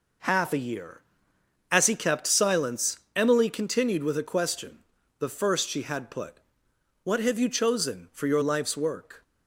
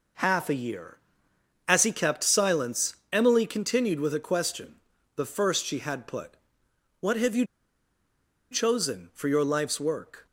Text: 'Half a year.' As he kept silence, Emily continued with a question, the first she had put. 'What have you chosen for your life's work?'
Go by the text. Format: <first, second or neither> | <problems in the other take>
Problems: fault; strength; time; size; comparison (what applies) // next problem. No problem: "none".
first | pauses between "you" and "chosen"; at 7.4 s; 1.0 s long